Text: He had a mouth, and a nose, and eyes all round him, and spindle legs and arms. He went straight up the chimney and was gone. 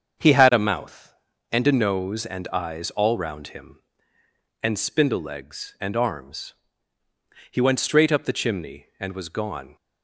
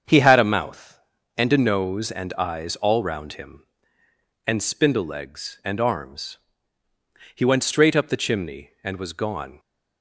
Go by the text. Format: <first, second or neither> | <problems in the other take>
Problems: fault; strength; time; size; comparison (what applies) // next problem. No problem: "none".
neither | starts louder than the rest; the same in both